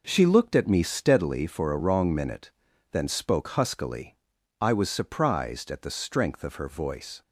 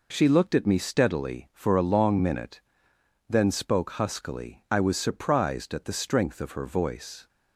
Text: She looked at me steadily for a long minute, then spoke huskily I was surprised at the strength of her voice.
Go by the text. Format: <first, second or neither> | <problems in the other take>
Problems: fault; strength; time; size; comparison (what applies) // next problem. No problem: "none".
second | says "wrong" for "long"; at 1.7 s // pauses between "huskily" and "I"; at 4.1 s; 0.42 s long